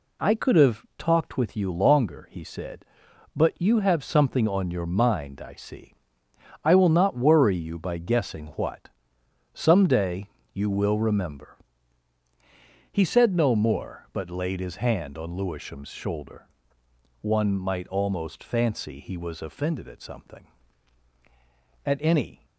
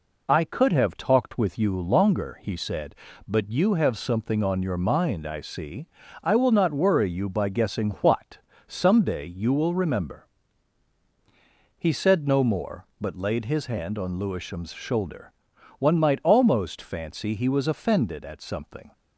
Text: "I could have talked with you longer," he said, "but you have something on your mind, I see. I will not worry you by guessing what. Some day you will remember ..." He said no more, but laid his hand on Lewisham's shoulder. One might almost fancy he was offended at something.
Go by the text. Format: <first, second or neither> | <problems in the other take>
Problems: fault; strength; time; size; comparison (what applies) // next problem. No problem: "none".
second | pauses between "day" and "you"; slight; at 10.2 s; 0.24 s long // goes on to say "At any"; noticeable; from 21.8 s on; 0.62 s long